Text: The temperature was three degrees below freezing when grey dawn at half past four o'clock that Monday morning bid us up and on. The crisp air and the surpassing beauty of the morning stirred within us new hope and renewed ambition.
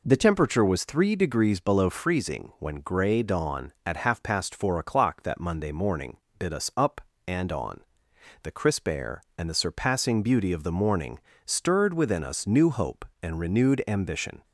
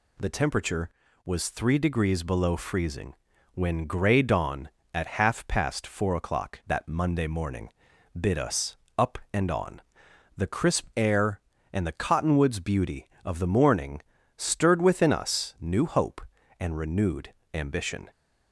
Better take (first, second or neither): first